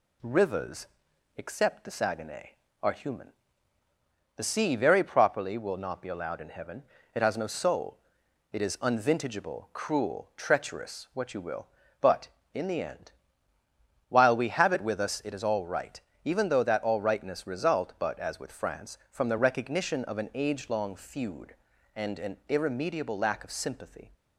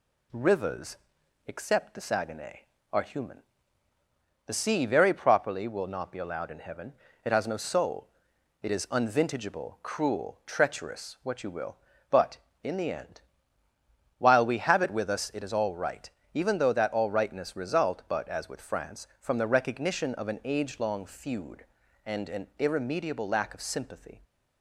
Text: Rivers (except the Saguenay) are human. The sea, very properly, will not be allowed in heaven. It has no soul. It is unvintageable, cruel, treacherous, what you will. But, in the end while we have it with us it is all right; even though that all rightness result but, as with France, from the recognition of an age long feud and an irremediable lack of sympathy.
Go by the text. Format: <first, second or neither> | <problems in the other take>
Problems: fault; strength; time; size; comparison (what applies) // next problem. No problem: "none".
neither | pauses between "end" and "while"; noticeable; the same in both